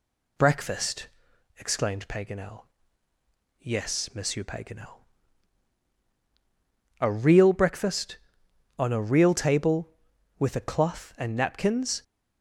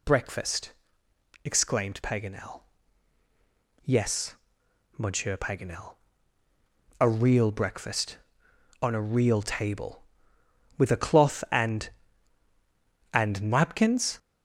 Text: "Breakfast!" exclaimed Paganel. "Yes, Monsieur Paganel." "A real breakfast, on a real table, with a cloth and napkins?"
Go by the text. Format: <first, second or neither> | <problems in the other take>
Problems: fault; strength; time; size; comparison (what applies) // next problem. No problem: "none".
first | says "and" twice; at 13.1 s